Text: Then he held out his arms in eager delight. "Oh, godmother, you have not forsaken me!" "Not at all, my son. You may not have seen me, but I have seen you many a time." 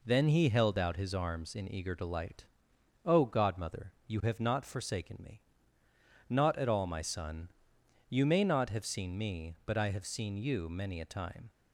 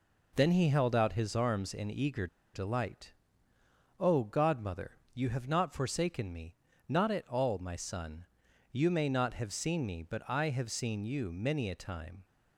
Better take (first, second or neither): first